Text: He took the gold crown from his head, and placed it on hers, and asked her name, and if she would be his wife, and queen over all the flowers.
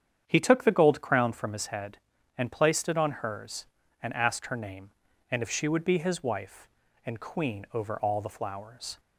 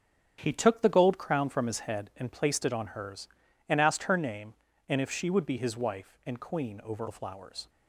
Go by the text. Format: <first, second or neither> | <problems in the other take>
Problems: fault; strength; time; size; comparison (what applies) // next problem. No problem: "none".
first | starts louder than the rest; strong; until 1.4 s; 8 dB; strong in the first // skips "all"; at 7.0 s